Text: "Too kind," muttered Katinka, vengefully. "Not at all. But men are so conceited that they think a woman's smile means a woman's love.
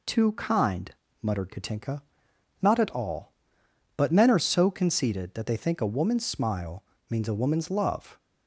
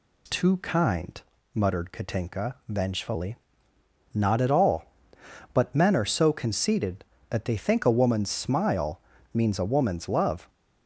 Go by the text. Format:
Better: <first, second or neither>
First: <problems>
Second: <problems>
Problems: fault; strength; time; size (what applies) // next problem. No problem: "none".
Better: second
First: skips "vengefully"; at 2.3 s // pauses between "smile" and "means"; slight; at 6.8 s; 0.26 s long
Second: pauses between "smile" and "means"; slight; at 9.0 s; 0.32 s long